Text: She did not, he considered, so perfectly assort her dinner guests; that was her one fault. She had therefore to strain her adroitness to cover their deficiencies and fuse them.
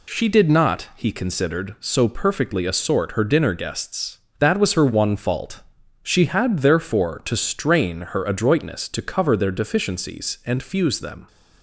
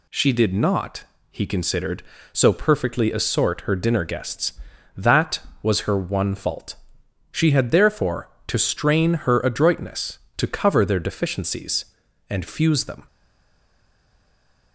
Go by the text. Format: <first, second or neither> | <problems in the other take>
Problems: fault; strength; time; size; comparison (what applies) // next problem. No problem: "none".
first | stays silent after the last word; noticeable; from 13.0 s on; 1.7 s long